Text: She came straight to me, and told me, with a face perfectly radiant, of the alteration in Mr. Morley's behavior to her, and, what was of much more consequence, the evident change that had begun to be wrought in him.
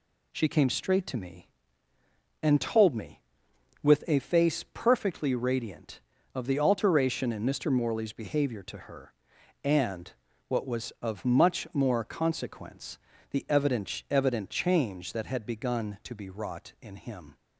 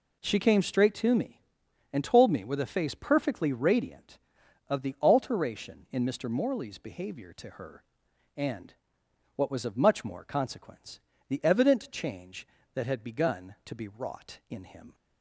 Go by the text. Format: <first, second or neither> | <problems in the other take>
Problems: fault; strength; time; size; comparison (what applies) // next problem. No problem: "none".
second | says "evident" twice; at 14.0 s